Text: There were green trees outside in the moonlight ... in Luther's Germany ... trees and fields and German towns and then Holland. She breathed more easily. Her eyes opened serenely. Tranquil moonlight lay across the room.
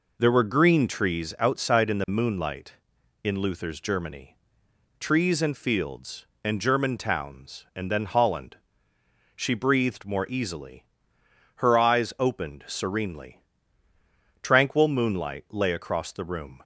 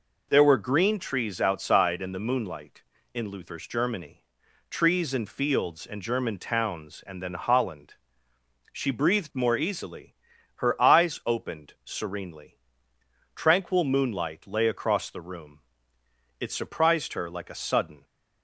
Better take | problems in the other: first | goes on to say "It surprised her like a sudden"; from 16.4 s on; 1.6 s long

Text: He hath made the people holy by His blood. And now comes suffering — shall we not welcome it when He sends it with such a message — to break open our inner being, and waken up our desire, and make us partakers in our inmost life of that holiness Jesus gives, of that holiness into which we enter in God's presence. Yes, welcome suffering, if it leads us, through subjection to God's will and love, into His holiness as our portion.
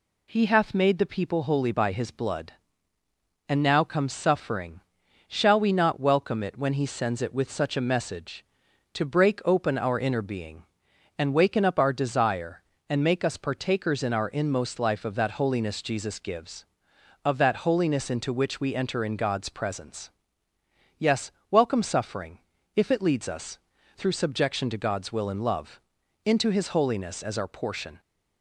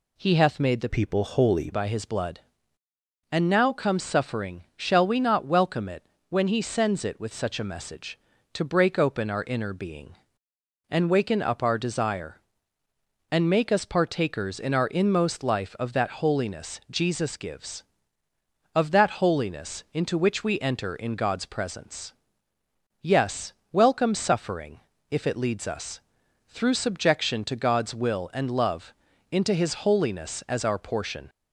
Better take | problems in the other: first | changes voice from "people" to "holy"; from 0.8 to 1.7 s; 0.9 s long // pauses between "it" and "when"; slight; at 6.0 s; 0.26 s long

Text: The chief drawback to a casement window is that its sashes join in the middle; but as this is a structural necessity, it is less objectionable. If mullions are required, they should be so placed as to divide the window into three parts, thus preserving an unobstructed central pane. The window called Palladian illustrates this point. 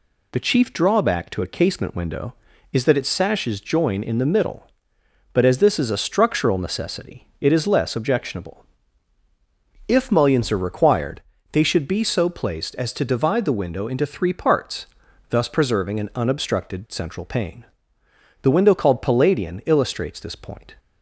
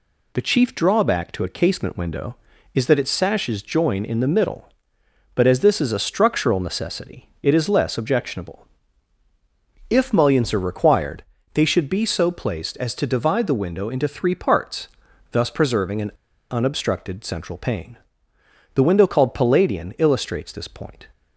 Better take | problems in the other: first | pauses between "an" and "unobstructed"; at 16.1 s; 0.39 s long

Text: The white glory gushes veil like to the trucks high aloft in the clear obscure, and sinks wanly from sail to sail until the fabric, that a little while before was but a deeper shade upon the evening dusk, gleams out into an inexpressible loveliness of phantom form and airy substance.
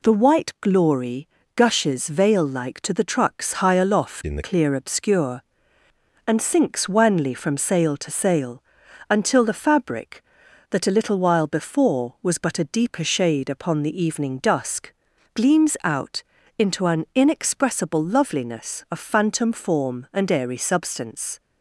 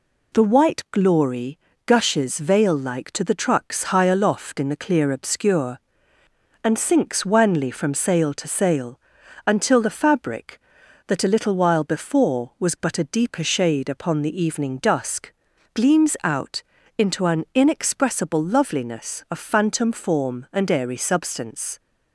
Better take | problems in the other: second | pauses between "glory" and "gushes"; slight; at 1.2 s; 0.26 s long; slight in the second // changes voice from "in" to "the"; from 4.2 to 4.4 s; 0.2 s long // pauses between "sail" and "until"; noticeable; at 8.6 s; 0.48 s long; noticeable in the second // pauses between "out" and "into"; slight; at 16.2 s; 0.34 s long; slight in the second

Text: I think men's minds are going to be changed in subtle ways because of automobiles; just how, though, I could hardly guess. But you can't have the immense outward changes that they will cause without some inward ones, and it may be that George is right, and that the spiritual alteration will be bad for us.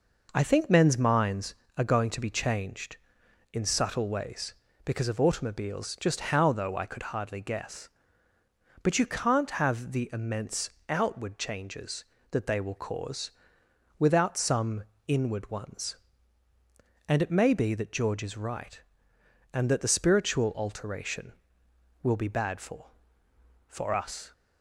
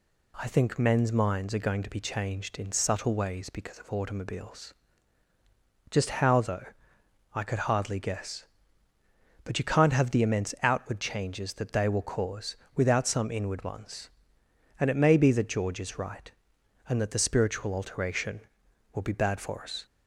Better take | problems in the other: second | pauses between "immense" and "outward"; slight; at 10.7 s; 0.18 s long // pauses between "cause" and "without"; noticeable; at 13.3 s; 0.66 s long; slight in the second // pauses between "some" and "inward"; slight; at 14.8 s; 0.24 s long // says "for" twice; at 23.6 s

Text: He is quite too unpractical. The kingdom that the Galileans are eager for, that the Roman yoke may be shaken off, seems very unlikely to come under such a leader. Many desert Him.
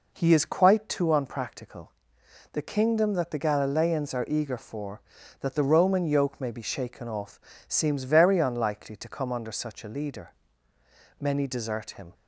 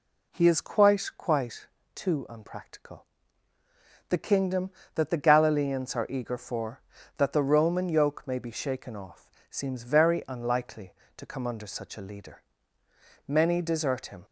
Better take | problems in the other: first | says "quite" twice; at 1.1 s

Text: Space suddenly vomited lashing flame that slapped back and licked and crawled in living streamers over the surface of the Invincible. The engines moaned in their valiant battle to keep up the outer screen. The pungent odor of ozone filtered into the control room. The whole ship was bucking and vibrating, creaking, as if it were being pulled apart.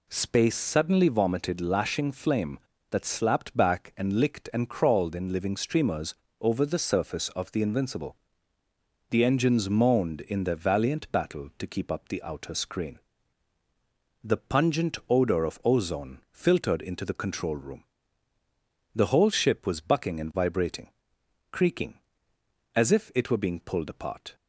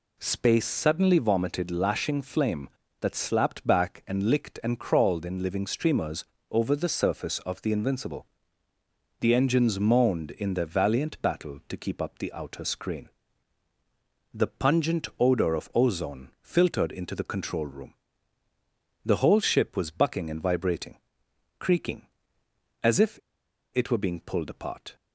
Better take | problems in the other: first | pauses between "streamers" and "over"; slight; at 6.2 s; 0.26 s long; slight in the first // pauses between "if" and "it"; noticeable; at 23.1 s; 0.56 s long

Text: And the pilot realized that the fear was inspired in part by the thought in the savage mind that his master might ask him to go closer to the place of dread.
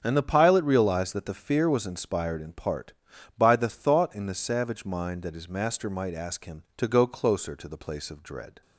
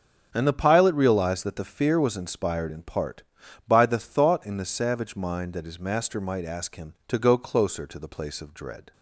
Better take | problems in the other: neither | starts louder than the rest; the same in both

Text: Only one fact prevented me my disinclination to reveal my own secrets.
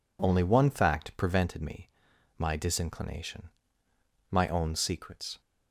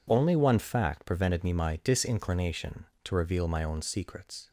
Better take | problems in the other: second | pauses between "me" and "my"; noticeable; at 1.8 s; 0.48 s long // skips "to reveal"; at 3.8 s

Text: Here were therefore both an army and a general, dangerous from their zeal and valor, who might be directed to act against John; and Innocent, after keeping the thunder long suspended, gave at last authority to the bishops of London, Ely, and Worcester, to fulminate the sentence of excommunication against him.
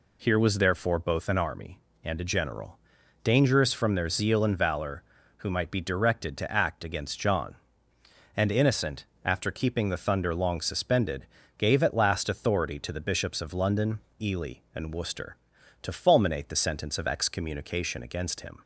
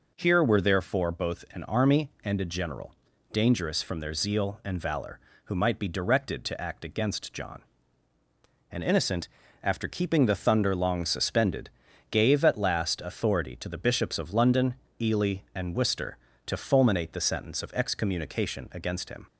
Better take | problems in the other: second | says "was" for "were"; at 0.3 s

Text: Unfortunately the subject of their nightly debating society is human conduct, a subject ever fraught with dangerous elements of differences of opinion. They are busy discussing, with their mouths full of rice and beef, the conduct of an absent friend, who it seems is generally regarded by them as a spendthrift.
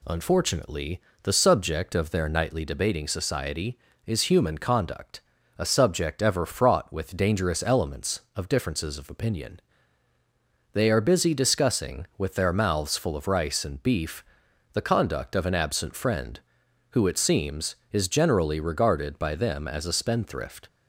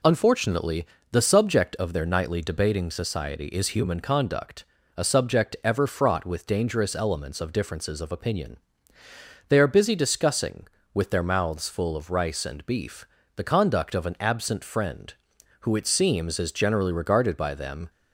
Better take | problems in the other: first | pauses between "Unfortunately" and "the"; slight; at 0.8 s; 0.26 s long; slight in the first // stops before "as a spendthrift"; at 17.8 s

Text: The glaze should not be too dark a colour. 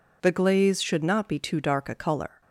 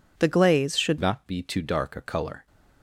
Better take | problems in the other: first | changes voice at "not"; from 1.0 s on; 1.4 s long

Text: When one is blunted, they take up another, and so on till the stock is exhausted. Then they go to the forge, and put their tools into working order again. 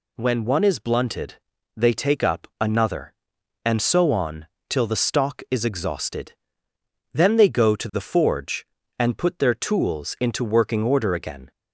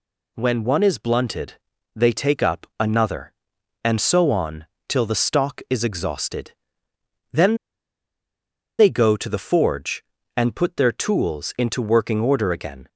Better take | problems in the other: first | pauses between "on" and "till"; slight; at 4.6 s; 0.22 s long; slight in the first // pauses between "Then" and "they"; strong; at 7.5 s; 1.2 s long

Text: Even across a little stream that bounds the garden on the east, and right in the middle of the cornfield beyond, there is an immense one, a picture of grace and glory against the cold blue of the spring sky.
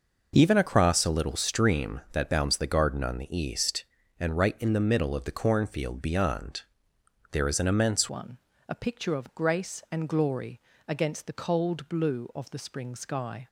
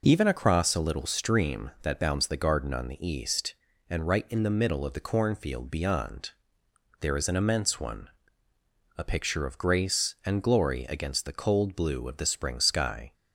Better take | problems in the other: second | changes voice at "one"; from 8.0 s on; 5.4 s long // pauses between "glory" and "against"; slight; at 10.5 s; 0.28 s long

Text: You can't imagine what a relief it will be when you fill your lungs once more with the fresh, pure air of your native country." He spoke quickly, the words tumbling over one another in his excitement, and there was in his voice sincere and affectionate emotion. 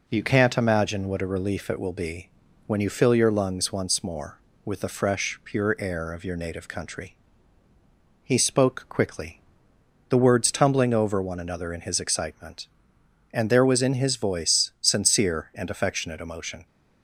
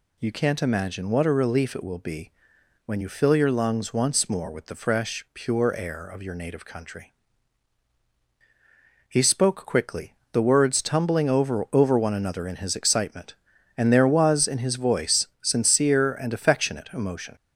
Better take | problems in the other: first | pauses between "be" and "when"; noticeable; at 2.3 s; 0.56 s long; also in the first // says "over" twice; at 11.7 s

